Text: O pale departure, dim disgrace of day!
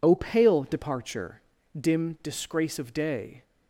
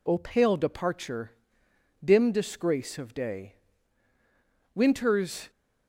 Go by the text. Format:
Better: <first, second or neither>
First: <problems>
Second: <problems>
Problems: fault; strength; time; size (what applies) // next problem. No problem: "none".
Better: first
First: none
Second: goes on to say "Winter's"; noticeable; from 4.7 s on; 0.74 s long